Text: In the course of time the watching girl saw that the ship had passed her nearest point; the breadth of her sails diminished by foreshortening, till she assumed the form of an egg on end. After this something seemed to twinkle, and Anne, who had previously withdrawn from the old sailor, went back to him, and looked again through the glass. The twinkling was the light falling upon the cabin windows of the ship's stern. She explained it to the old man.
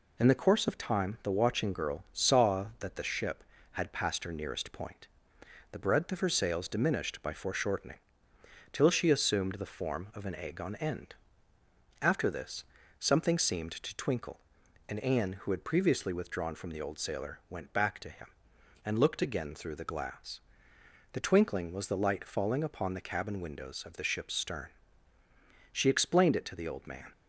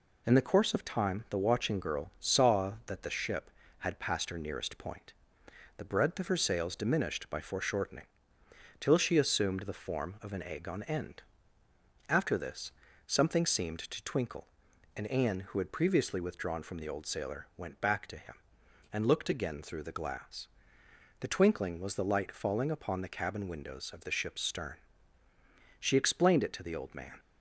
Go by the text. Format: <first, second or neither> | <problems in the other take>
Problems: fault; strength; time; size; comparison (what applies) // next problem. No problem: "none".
neither | pauses between "this" and "something"; slight; the same in both